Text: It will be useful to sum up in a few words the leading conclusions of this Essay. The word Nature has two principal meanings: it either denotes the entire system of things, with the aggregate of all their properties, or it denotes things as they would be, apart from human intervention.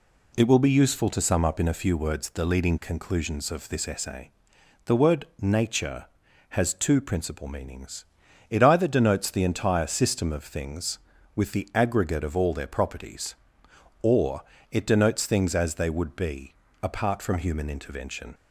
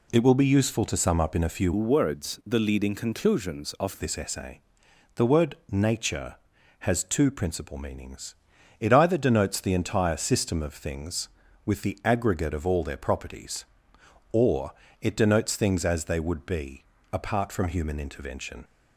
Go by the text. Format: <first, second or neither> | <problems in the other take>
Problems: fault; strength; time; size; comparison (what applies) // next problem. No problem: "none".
first | changes voice from "words" to "of"; from 1.7 to 3.9 s; 2.2 s long // pauses between "word" and "Nature"; slight; at 5.5 s; 0.16 s long; slight in the first // pauses between "or" and "it"; slight; at 14.7 s; 0.28 s long; slight in the first